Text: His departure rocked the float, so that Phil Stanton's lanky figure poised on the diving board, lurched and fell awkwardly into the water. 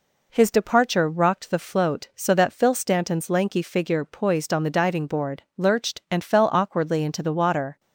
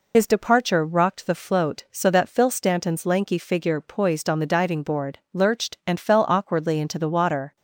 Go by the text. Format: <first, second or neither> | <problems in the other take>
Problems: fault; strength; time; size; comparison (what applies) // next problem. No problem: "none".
first | loses the start of "His"; at 0.1 s; 70 ms